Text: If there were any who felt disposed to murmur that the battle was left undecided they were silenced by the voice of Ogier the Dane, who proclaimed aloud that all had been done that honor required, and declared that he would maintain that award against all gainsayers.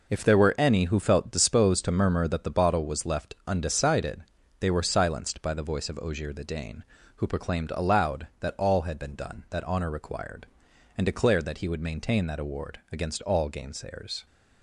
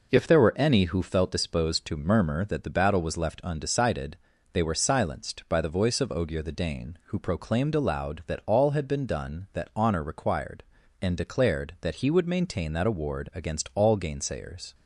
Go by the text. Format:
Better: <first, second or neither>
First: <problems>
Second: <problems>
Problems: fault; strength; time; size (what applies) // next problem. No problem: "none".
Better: second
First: says "bottle" for "battle"; at 2.4 s // pauses between "undecided" and "they"; slight; at 4.2 s; 0.36 s long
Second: pauses between "undecided" and "they"; at 4.1 s; 0.38 s long